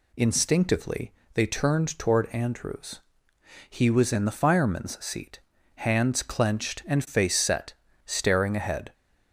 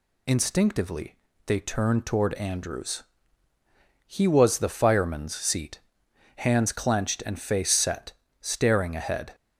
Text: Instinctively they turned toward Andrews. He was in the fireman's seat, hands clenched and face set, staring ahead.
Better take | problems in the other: first | pauses between "Instinctively" and "they"; slight; at 1.1 s; 0.30 s long; slight in the first // skips "in"; at 4.5 s

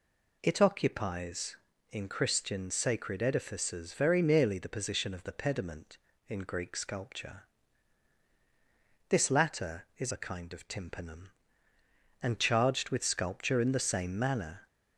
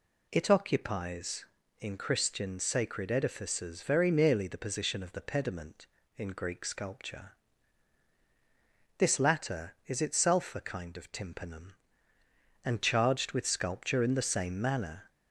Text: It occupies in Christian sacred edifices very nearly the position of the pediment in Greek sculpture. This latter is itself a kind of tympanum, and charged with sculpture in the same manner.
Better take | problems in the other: second | skips "itself"; at 10.1 s

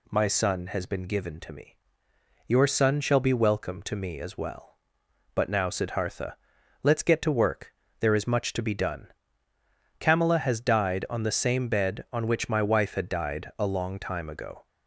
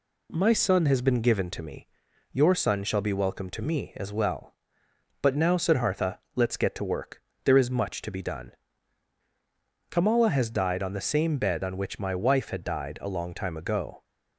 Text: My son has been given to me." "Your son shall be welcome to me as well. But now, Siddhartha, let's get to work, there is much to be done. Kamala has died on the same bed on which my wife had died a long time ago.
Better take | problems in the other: neither | none

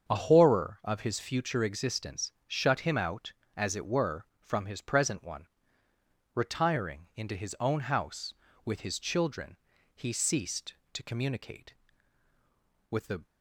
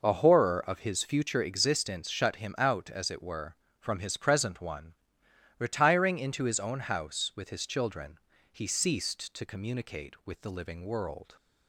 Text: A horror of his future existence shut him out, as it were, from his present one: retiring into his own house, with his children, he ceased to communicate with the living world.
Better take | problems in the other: second | starts louder than the rest; until 1.1 s; 7 dB // pauses between "existence" and "shut"; slight; at 2.3 s; 0.16 s long // stops before "living world"; at 13.2 s

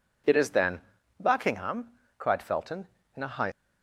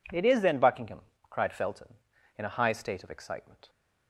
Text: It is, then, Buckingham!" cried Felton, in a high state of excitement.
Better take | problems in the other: second | stops before "state of excitement"; at 3.5 s

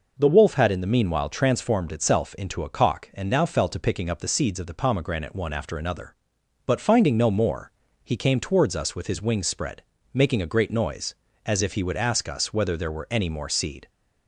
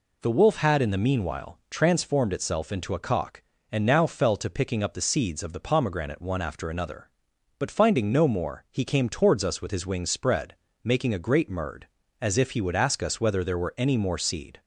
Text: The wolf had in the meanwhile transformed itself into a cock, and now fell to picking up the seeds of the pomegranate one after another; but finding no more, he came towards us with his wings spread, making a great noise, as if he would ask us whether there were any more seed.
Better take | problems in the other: first | says "murd" for "noise"; at 11.4 s

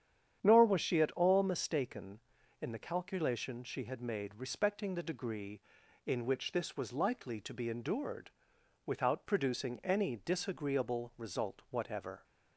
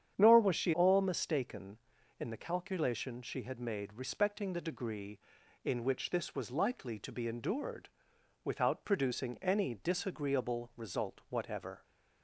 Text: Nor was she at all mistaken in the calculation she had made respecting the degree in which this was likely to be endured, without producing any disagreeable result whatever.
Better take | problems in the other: first | starts louder than the rest; strong; until 1.1 s; 9 dB; strong in the first // skips "at"; at 0.7 s

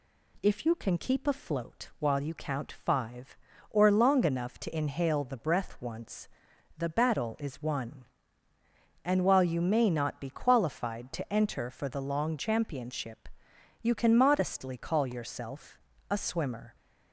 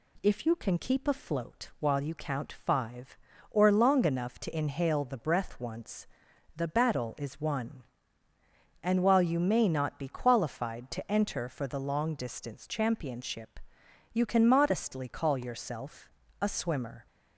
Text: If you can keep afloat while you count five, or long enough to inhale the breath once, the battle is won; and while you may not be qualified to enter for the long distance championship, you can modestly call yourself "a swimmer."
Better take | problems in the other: second | skips "distance"; at 12.3 s // pauses between "yourself" and "a"; slight; at 15.7 s; 0.32 s long; slight in the second

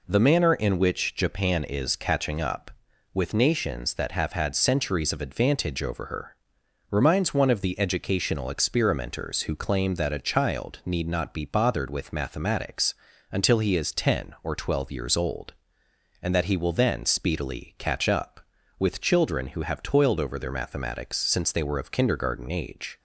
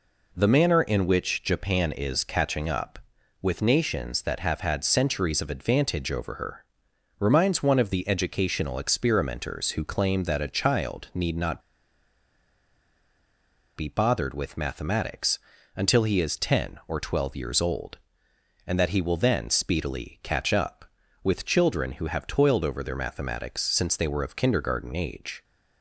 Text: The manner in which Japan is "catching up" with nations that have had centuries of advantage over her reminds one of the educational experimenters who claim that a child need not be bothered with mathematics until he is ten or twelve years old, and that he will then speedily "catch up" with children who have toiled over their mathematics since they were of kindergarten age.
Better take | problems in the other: first | pauses between "her" and "reminds"; noticeable; at 6.6 s; 0.54 s long; noticeable in the first // pauses between "not" and "be"; strong; at 11.6 s; 2.1 s long // pauses between "mathematics" and "until"; slight; at 15.3 s; 0.36 s long; slight in the first

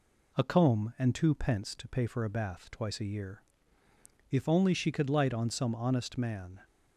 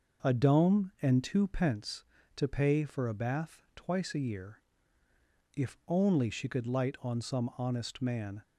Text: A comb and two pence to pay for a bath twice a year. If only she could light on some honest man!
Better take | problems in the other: first | says "dome" for "comb"; at 0.3 s

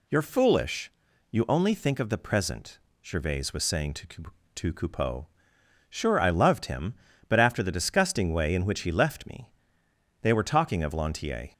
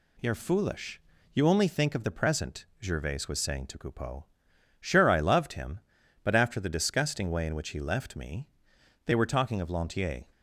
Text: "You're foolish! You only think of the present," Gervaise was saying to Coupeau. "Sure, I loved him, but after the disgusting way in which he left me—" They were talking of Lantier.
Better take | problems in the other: second | says "to" twice; at 4.5 s

